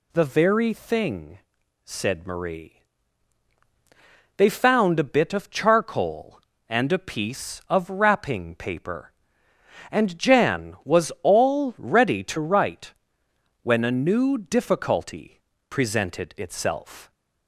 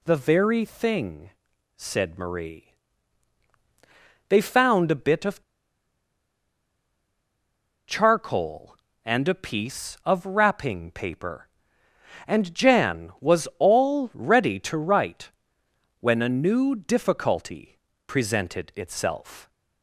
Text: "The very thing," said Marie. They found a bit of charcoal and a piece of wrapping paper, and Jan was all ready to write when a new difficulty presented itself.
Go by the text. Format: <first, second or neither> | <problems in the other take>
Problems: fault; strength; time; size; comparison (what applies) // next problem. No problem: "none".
first | pauses between "of" and "charcoal"; strong; at 5.4 s; 2.4 s long // pauses between "write" and "when"; noticeable; at 15.3 s; 0.68 s long; noticeable in the first // pauses between "difficulty" and "presented"; slight; at 17.7 s; 0.28 s long; slight in the first